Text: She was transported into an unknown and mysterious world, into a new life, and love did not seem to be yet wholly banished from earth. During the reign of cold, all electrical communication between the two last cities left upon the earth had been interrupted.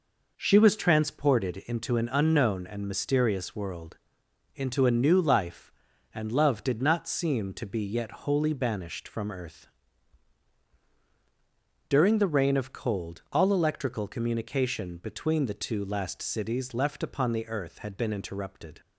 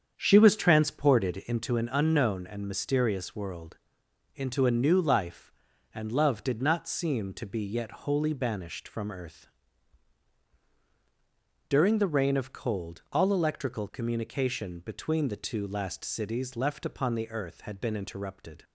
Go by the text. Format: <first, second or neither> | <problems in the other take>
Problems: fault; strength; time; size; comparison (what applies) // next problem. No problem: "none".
first | starts louder than the rest; strong; until 1.7 s; 7.5 dB